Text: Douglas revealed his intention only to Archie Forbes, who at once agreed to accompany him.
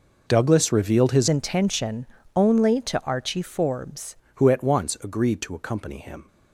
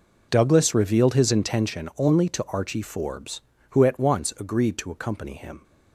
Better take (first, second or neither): second